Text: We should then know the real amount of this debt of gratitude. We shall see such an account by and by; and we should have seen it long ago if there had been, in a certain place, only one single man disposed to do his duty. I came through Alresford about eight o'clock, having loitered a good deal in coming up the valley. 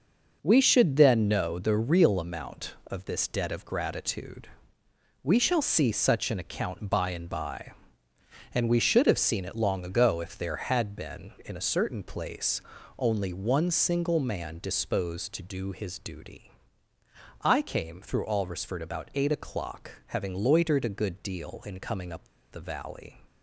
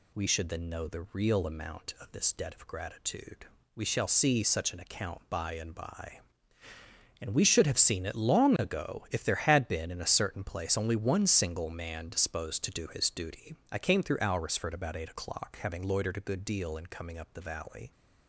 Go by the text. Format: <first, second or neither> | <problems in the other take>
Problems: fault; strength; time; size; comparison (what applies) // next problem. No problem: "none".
second | pauses between "up" and "the"; slight; at 22.2 s; 0.26 s long